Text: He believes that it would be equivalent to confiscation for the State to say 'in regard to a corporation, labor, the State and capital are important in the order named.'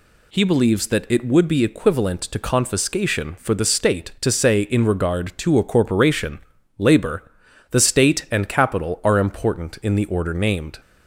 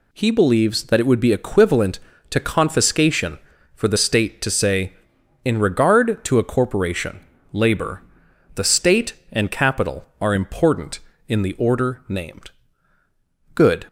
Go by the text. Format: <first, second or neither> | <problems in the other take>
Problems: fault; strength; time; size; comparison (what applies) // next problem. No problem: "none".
first | goes on to say "Good"; slight; from 13.5 s on; 0.32 s long